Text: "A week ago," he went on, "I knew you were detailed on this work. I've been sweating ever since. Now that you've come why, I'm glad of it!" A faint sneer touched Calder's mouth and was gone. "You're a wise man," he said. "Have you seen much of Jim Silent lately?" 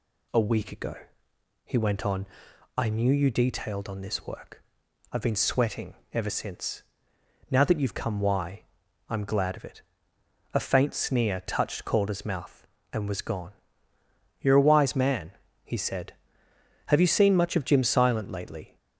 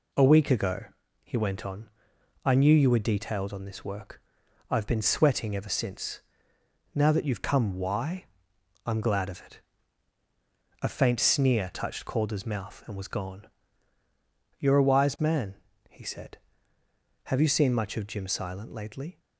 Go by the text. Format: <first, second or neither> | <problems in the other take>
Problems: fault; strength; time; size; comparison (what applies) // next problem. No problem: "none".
second | skips "were"; at 3.3 s // pauses between "sweating" and "ever"; slight; at 5.9 s; 0.18 s long